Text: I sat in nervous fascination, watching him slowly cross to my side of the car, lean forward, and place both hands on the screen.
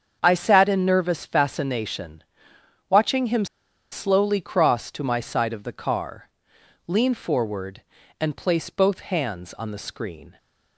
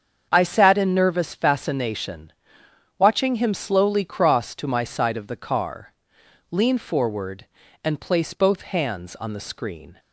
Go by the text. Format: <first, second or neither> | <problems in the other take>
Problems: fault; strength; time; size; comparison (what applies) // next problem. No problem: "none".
second | starts louder than the rest; strong; until 1.2 s; 7 dB; strong in the second // pauses between "him" and "slowly"; noticeable; at 3.4 s; 0.46 s long